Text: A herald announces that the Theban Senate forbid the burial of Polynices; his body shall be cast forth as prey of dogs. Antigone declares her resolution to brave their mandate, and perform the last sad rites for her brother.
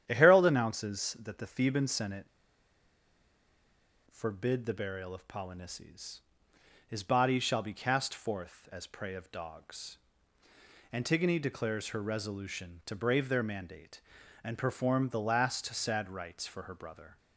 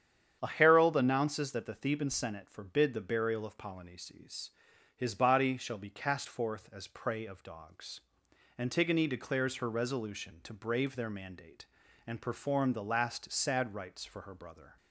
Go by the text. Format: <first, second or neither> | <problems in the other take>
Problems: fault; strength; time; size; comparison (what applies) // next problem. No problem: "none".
second | starts louder than the rest; strong; until 1.0 s; 10 dB; strong in the second // pauses between "Senate" and "forbid"; strong; at 2.2 s; 1.8 s long